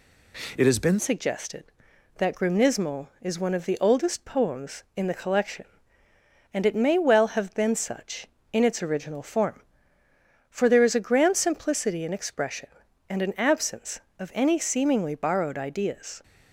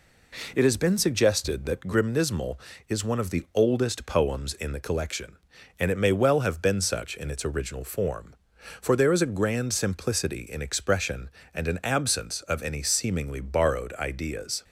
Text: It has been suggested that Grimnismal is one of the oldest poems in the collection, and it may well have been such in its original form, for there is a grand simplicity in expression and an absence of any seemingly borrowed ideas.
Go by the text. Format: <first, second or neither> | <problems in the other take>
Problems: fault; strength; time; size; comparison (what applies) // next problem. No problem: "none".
second | changes voice at "suggested"; from 0.9 s on; 15.3 s long